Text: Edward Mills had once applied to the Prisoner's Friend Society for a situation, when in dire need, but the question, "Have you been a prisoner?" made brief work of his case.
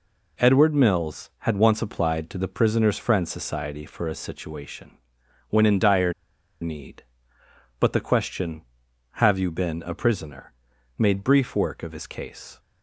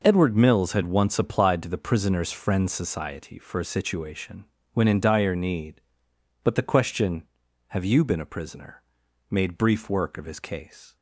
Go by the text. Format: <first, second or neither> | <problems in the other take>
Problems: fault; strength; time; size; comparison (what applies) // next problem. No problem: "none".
second | pauses between "dire" and "need"; noticeable; at 6.1 s; 0.48 s long